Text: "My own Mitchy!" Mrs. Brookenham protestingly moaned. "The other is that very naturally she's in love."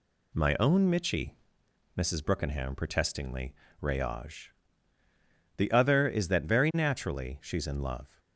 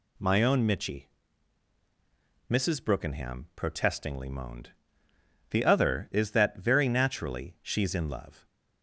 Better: second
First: says "rayage" for "moaned"; at 3.8 s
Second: none

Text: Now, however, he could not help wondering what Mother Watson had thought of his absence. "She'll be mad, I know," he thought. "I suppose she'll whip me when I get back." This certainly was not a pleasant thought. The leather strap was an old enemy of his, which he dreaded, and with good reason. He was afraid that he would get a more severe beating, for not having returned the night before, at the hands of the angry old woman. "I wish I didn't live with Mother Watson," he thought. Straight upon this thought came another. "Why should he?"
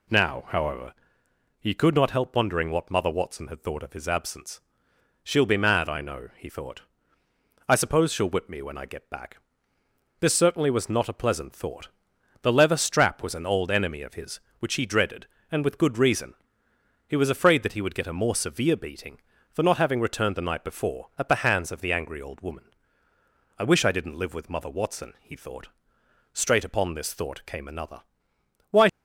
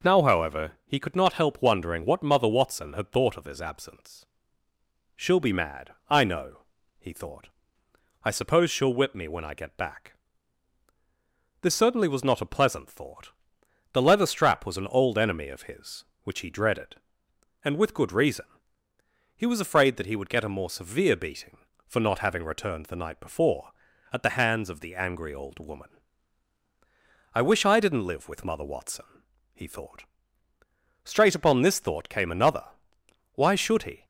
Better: second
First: stops before "should he"; at 28.8 s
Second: none

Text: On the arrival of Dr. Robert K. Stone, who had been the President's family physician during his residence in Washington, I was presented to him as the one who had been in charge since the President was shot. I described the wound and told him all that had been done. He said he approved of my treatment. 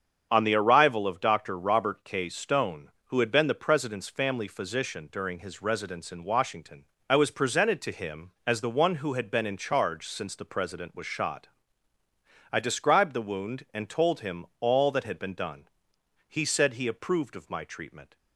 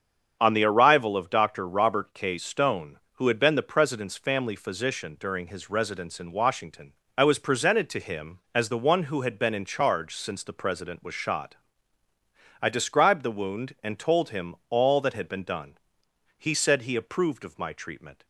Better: neither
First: starts louder than the rest; strong; until 1.3 s; 7.5 dB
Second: starts louder than the rest; strong; until 1.4 s; 7.5 dB

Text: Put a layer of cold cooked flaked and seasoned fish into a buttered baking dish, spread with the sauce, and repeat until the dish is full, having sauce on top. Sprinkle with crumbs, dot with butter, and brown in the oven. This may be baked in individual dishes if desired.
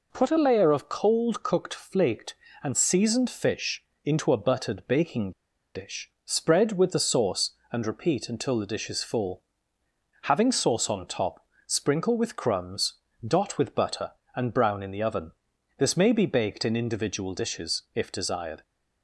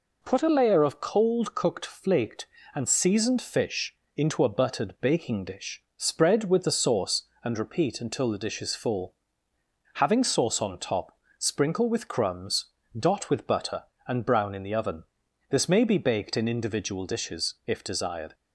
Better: second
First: pauses between "fish" and "into"; slight; at 3.8 s; 0.20 s long // pauses between "baking" and "dish"; at 5.3 s; 0.44 s long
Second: pauses between "fish" and "into"; slight; at 3.9 s; 0.20 s long

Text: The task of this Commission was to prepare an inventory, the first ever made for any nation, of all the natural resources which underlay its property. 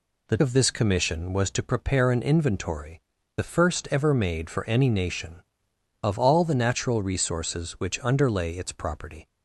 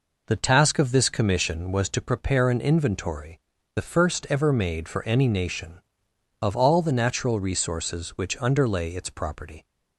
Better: second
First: skips "task"; at 0.3 s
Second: none

